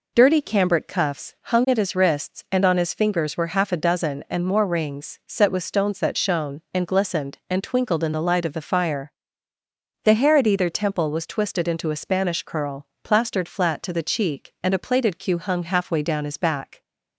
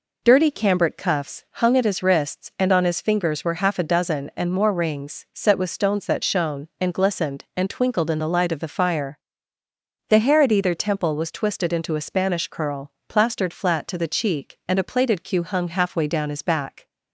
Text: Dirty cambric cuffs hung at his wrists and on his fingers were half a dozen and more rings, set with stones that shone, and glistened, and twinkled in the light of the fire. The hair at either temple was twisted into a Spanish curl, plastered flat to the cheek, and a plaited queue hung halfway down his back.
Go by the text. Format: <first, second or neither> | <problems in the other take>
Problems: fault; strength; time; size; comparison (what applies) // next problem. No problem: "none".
neither | none